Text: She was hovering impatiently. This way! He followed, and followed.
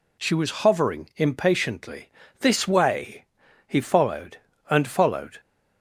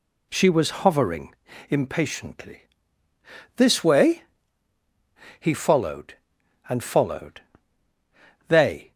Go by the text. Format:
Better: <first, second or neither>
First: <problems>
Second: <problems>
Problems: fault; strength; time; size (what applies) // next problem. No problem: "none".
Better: first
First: none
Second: pauses between "hovering" and "impatiently"; slight; at 1.3 s; 0.34 s long // goes on to say "They"; slight; from 8.4 s on; 0.44 s long